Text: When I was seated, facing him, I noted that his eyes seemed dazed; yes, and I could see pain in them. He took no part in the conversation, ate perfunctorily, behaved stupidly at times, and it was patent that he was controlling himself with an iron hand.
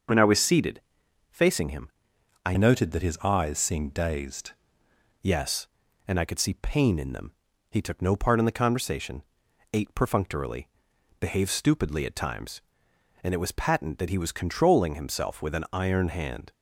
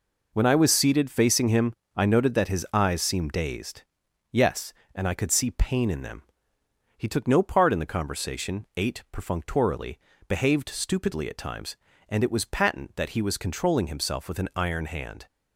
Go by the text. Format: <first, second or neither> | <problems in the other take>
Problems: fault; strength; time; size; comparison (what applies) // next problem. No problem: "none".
second | starts louder than the rest; until 1.6 s; 6 dB // changes voice from "noted" to "dazed"; from 2.5 to 4.5 s; 2.0 s long